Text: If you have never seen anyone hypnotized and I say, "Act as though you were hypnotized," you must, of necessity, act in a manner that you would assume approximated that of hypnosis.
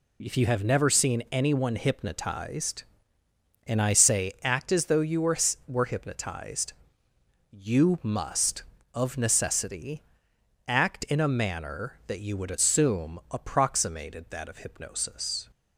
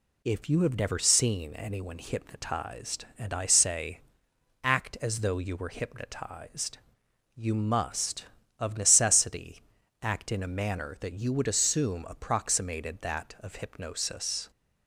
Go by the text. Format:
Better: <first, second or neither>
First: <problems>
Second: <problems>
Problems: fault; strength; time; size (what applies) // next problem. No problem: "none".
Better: second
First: says "were" twice; at 5.6 s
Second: none